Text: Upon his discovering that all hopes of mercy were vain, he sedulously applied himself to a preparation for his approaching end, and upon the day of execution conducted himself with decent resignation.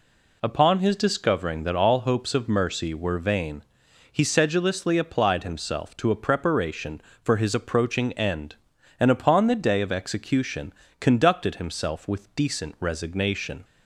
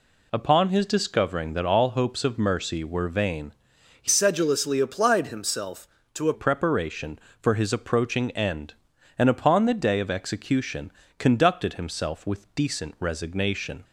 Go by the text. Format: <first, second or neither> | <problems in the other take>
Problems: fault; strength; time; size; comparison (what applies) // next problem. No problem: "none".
first | changes voice from "sedulously" to "a"; from 4.0 to 6.3 s; 2.3 s long // pauses between "execution" and "conducted"; slight; at 10.9 s; 0.26 s long; slight in the first